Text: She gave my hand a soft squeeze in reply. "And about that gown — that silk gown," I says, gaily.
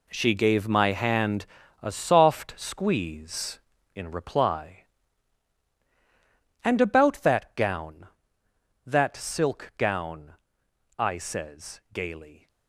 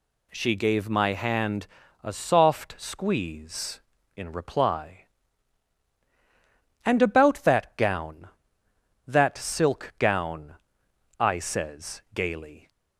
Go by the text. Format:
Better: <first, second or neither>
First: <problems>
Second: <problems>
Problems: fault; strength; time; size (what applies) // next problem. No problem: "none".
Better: second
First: gets quieter; strong; throughout; 12 dB // pauses between "hand" and "a"; slight; at 1.4 s; 0.36 s long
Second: pauses between "hand" and "a"; slight; at 1.6 s; 0.36 s long